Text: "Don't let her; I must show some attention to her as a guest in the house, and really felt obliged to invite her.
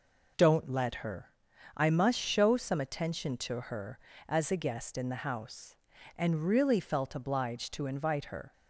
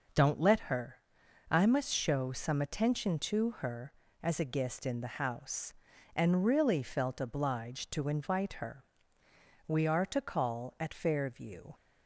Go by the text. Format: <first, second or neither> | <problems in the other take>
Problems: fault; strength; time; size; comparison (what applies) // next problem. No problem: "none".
first | goes on to say "We are to call at Fairview"; strong; from 9.6 s on; 2.0 s long